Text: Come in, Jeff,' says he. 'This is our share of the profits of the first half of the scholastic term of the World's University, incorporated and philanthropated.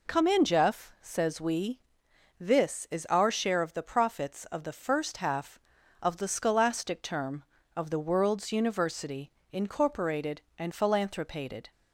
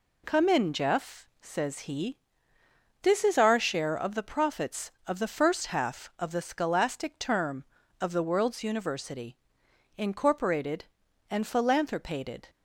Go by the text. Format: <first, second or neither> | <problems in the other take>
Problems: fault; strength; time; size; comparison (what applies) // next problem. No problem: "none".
second | says "we" for "he"; at 1.4 s